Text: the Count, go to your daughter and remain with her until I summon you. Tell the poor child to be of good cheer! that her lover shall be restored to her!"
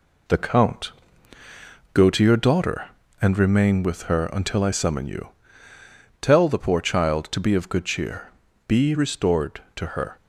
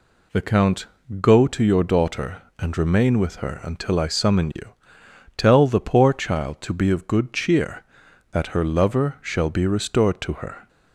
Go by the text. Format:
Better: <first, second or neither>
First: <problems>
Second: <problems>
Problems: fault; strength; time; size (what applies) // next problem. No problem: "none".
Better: second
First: skips "that her lover shall"; at 8.4 s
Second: none